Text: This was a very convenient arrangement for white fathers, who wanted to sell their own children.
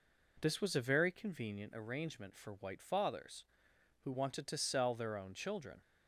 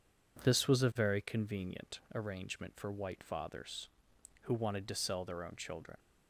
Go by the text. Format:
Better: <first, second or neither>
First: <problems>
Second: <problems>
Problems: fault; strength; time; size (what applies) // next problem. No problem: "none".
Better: neither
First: none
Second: none